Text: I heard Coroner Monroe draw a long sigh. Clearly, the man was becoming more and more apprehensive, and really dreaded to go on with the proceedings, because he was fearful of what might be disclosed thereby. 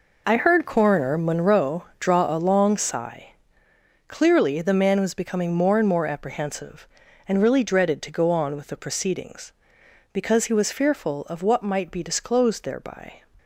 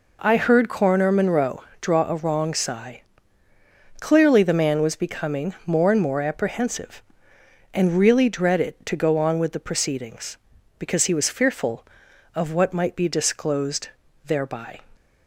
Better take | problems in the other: first | pauses between "Monroe" and "draw"; slight; at 1.6 s; 0.16 s long; slight in the first // says "wrong" for "long"; at 2.1 s // pauses between "disclosed" and "thereby"; at 13.8 s; 0.38 s long

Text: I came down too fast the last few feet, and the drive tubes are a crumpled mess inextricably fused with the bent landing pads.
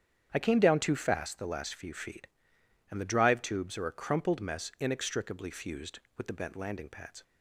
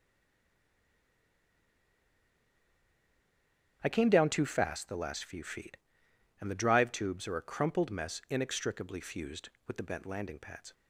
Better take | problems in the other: first | stays silent before the first word; strong; until 3.8 s; 3.8 s long // starts louder than the rest; strong; until 4.8 s; 8.5 dB; strong in the first

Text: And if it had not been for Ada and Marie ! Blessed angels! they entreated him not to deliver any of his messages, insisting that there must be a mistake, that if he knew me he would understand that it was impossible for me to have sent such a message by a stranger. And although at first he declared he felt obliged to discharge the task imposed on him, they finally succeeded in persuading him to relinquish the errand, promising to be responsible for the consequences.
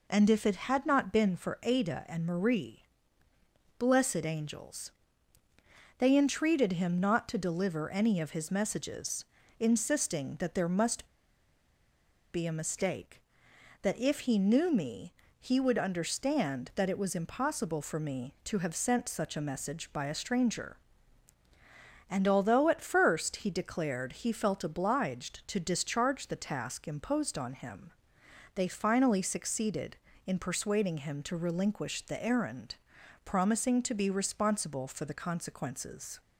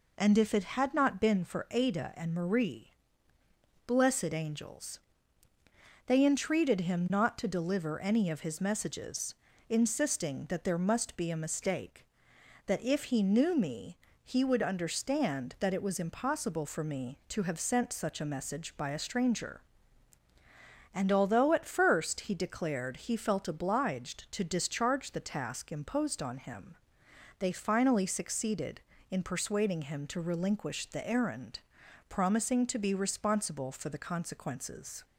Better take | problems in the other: second | pauses between "must" and "be"; strong; at 11.0 s; 1.2 s long // pauses between "me" and "he"; slight; at 15.1 s; 0.26 s long; slight in the second

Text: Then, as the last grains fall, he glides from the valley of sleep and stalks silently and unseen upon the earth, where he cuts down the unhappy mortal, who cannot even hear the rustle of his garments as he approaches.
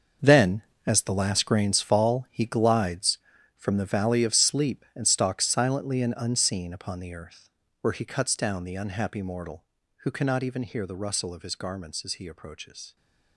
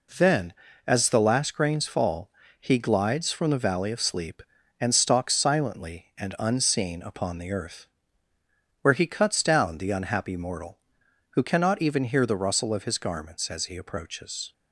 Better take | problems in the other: second | gets quieter; strong; throughout; 13 dB

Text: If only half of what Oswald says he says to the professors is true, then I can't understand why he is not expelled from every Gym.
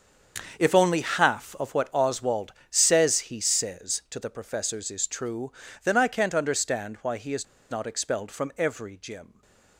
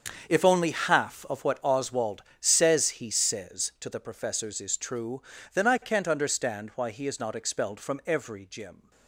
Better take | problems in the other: second | starts louder than the rest; until 1.6 s; 7 dB; also in the second // pauses between "Oswald" and "says"; slight; at 2.5 s; 0.16 s long; slight in the second // pauses between "is" and "not"; slight; at 7.4 s; 0.26 s long // stays silent after the last word; slight; from 9.2 s on; 0.5 s long

